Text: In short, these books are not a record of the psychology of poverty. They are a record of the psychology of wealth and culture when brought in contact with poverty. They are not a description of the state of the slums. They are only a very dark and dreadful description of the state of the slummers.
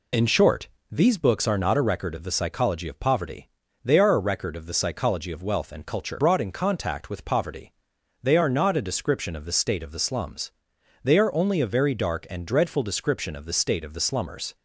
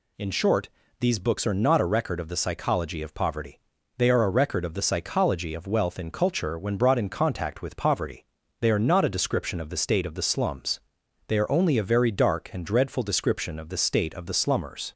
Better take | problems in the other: second | skips "when"; at 6.1 s

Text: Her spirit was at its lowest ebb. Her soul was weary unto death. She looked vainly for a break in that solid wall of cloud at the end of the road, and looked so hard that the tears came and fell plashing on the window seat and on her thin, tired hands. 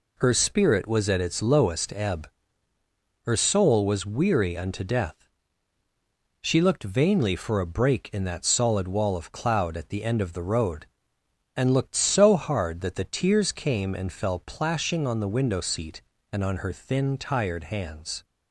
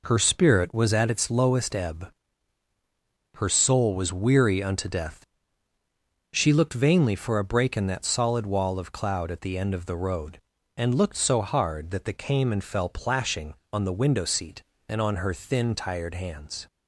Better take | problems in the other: first | skips "tears"; at 12.1 s

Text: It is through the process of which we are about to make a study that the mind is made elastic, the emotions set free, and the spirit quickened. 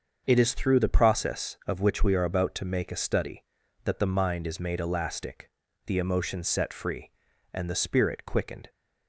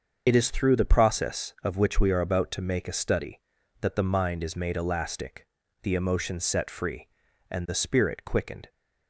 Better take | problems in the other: first | loses the start of "It"; at 0.2 s; 45 ms // starts louder than the rest; until 1.2 s; 6.5 dB; also in the first

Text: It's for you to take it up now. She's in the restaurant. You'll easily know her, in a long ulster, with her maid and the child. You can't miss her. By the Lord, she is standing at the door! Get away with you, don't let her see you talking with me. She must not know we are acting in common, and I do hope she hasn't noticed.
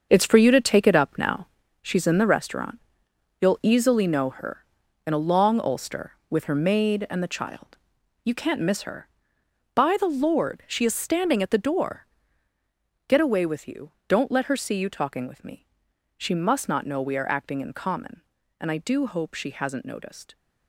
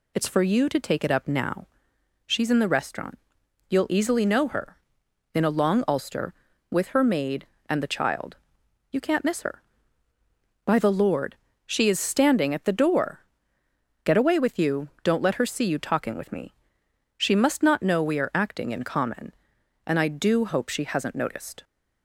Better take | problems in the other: second | gets quieter; strong; throughout; 10 dB

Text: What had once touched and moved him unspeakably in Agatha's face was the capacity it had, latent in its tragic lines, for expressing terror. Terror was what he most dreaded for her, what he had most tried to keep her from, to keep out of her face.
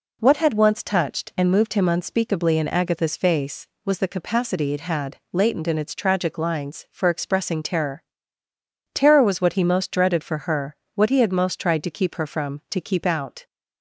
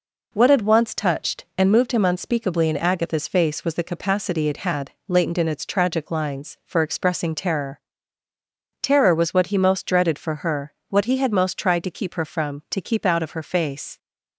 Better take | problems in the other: second | stops before "of her face"; at 13.4 s

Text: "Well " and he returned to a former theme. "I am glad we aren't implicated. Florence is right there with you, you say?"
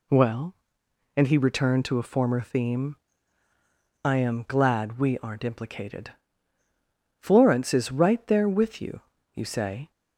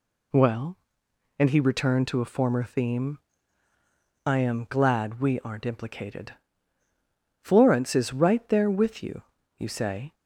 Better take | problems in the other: neither | none

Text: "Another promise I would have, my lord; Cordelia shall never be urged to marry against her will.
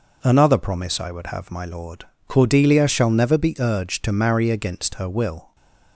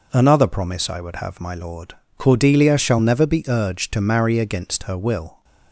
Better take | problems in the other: neither | none

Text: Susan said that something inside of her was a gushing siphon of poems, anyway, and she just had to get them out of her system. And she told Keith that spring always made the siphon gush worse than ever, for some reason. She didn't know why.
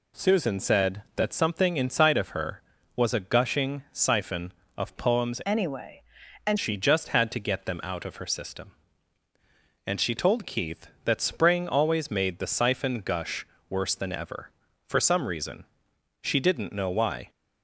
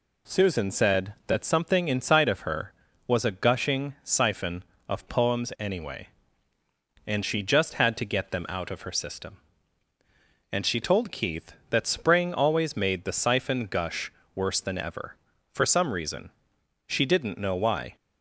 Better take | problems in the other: second | changes voice from "anyway" to "and"; from 5.4 to 6.5 s; 1.1 s long // pauses between "gush" and "worse"; slight; at 13.4 s; 0.24 s long; slight in the second

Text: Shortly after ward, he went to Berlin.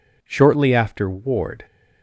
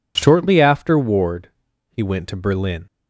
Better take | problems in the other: second | stops before "he went to Berlin"; at 1.6 s

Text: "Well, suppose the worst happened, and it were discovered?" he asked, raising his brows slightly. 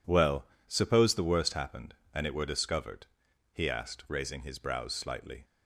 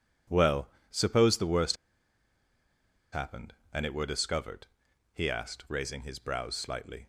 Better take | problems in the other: first | pauses between "worst" and "happened"; strong; at 1.7 s; 1.3 s long

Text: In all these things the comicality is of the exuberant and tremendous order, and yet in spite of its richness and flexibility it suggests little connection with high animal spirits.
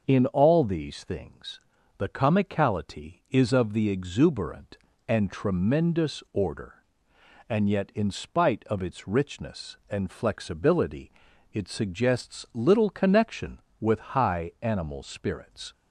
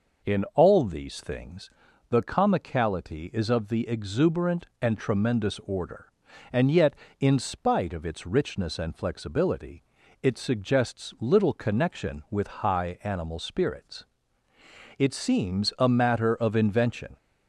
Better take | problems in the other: first | pauses between "things" and "the"; at 1.7 s; 0.38 s long; slight in the first // pauses between "flexibility" and "it"; at 9.8 s; 0.38 s long; also in the first // goes on to say "It seems a matter of invention"; strong; from 14.9 s on; 2.2 s long

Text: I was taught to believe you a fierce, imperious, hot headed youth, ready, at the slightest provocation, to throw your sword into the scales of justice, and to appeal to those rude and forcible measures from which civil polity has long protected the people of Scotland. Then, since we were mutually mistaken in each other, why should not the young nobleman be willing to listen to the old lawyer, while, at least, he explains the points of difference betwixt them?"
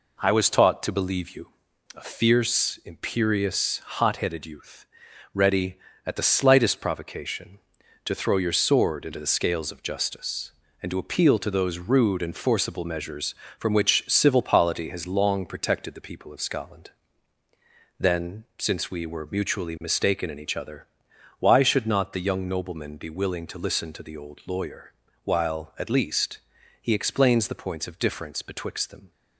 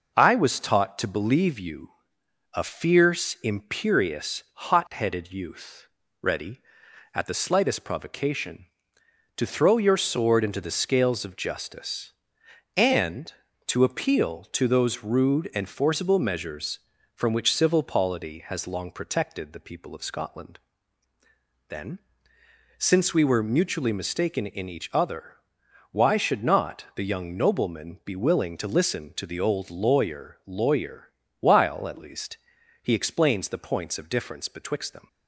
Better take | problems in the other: first | pauses between "you" and "a"; noticeable; at 1.9 s; 0.62 s long; noticeable in the first // says "lawyer" twice; at 30.4 s

